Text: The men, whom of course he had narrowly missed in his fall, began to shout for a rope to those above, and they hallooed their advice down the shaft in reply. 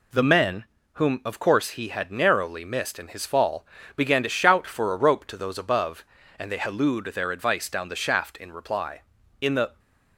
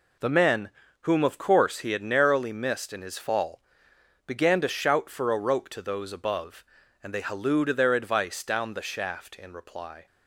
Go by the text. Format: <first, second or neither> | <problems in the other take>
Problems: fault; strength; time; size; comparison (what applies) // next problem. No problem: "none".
second | goes on to say "In the"; slight; from 9.4 s on; 0.38 s long